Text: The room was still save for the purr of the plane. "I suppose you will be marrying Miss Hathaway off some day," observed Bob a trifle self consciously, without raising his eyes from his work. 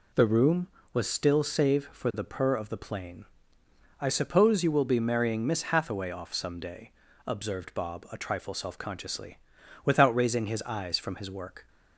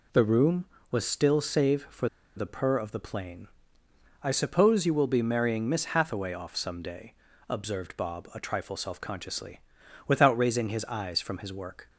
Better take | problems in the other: first | pauses between "for" and "the"; slight; at 2.0 s; 0.28 s long

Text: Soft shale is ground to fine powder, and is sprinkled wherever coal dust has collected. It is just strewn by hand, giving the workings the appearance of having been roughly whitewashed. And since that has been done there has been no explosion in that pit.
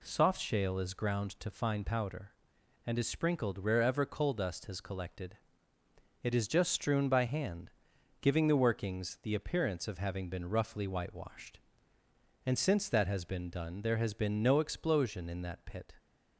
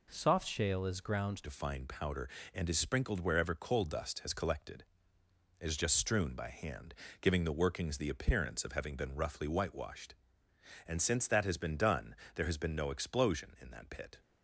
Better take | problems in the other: first | changes voice at "to"; from 1.4 s on; 12.8 s long // pauses between "done" and "there"; slight; at 12.1 s; 0.18 s long

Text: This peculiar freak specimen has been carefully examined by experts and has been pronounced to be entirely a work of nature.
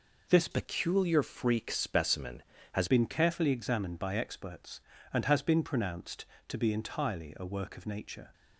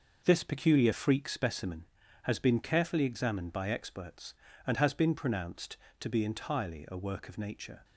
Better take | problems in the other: second | changes voice from "peculiar" to "has"; from 0.5 to 2.8 s; 2.3 s long

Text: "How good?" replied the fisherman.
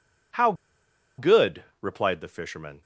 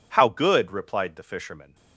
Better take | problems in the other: second | pauses between "How" and "good"; noticeable; at 0.5 s; 0.65 s long

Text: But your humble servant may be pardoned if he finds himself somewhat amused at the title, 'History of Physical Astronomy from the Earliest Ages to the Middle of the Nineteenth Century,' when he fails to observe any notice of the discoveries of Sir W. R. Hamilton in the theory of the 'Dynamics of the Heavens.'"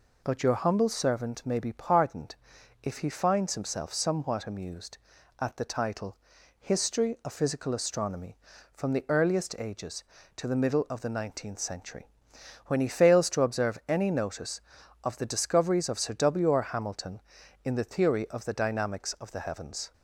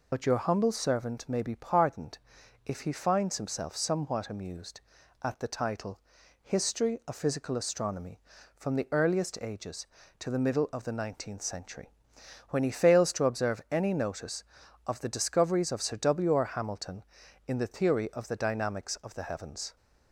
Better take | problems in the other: first | loses the start of "But"; at 0.1 s; 50 ms // pauses between "pardoned" and "if"; noticeable; at 2.1 s; 0.48 s long; noticeable in the first

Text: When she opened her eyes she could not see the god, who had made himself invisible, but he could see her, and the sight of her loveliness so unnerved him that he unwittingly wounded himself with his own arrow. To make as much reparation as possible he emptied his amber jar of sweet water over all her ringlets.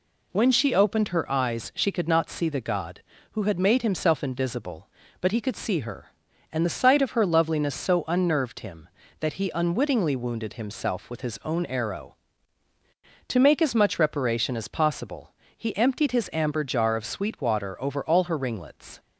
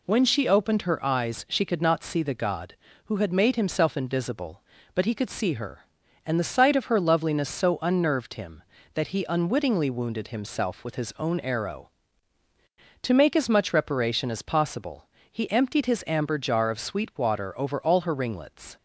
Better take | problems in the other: neither | pauses between "possible" and "he"; slight; the same in both

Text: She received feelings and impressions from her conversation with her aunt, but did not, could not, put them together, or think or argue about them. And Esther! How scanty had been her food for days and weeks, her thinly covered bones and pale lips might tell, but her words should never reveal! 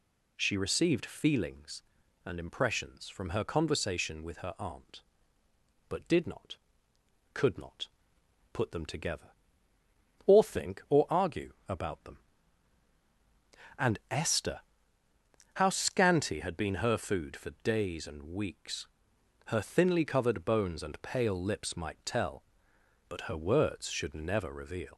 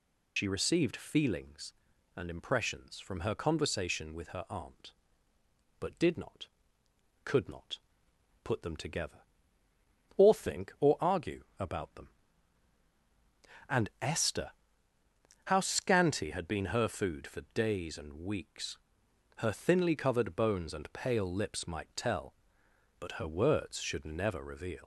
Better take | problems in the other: first | loses the start of "She"; at 0.3 s; 95 ms // pauses between "argue" and "about"; slight; at 11.4 s; 0.16 s long; slight in the first

